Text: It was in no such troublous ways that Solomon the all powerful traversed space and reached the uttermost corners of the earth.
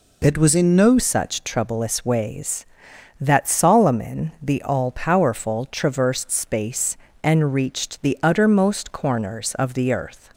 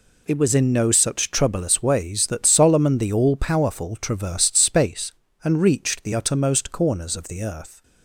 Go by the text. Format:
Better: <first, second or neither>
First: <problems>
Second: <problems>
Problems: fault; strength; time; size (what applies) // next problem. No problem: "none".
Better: second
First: changes voice at "such"; from 0.9 s on; 9.4 s long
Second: none